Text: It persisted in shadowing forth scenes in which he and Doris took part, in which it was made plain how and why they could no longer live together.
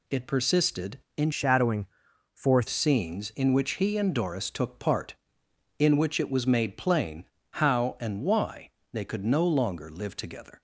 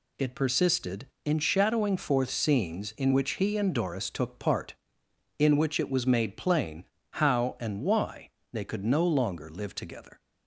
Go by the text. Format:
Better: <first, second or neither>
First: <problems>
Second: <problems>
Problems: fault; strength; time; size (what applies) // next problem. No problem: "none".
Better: second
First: changes voice from "shadowing" to "forth"; from 1.3 to 2.6 s; 1.3 s long // pauses between "shadowing" and "forth"; noticeable; at 1.8 s; 0.46 s long // pauses between "plain" and "how"; slight; at 7.2 s; 0.26 s long // pauses between "why" and "they"; slight; at 8.6 s; 0.22 s long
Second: pauses between "plain" and "how"; slight; at 6.8 s; 0.26 s long // pauses between "why" and "they"; slight; at 8.2 s; 0.22 s long